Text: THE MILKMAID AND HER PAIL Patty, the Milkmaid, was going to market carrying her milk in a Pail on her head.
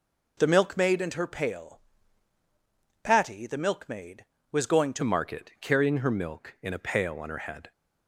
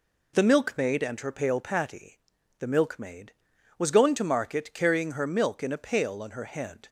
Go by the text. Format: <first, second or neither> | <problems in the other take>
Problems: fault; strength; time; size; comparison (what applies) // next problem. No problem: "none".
second | pauses between "PAIL" and "Patty"; at 1.8 s; 1.2 s long // changes voice at "market"; from 5.0 s on; 2.7 s long